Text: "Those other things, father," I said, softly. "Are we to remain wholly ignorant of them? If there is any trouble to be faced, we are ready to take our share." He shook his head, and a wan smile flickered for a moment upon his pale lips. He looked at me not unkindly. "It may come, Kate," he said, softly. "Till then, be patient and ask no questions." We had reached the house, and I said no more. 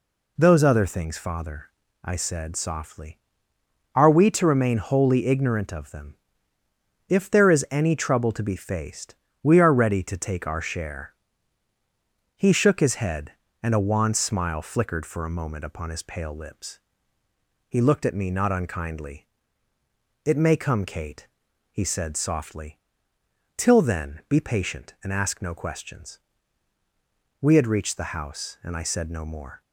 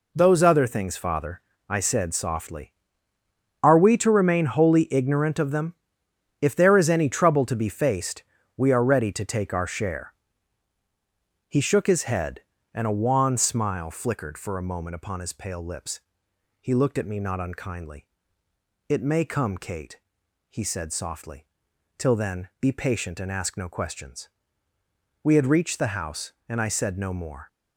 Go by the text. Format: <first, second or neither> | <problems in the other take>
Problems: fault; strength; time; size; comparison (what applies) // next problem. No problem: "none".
neither | none